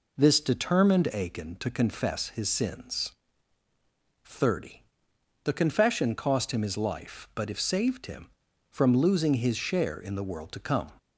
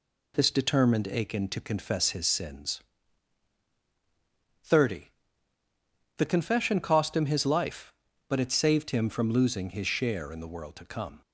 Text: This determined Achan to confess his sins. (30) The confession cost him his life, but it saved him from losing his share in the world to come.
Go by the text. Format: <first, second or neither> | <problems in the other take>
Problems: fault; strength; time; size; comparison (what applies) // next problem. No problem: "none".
second | says "if" for "it"; at 7.4 s